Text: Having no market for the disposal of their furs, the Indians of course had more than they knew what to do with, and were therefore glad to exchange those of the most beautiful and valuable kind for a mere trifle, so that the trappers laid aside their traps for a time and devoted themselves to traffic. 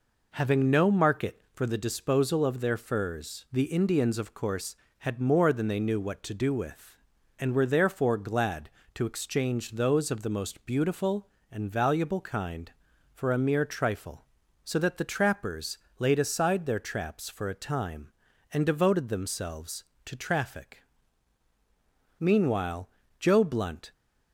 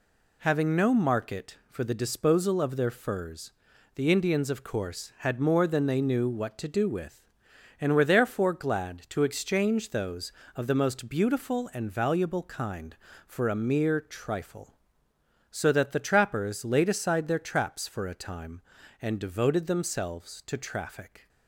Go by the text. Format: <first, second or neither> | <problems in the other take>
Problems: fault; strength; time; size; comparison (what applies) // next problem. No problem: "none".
second | pauses between "trappers" and "laid"; slight; at 15.7 s; 0.22 s long // goes on to say "Meanwhile Joe Blunt"; strong; from 22.1 s on; 1.7 s long